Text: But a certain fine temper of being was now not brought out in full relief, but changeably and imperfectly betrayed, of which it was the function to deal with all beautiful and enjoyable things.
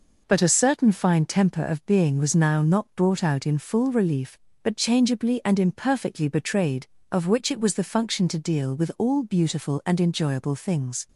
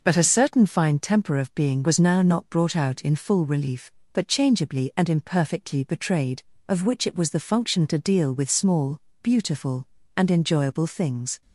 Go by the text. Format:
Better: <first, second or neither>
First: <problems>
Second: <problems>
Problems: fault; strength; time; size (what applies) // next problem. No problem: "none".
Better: first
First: none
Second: says "small" for "all"; at 8.4 s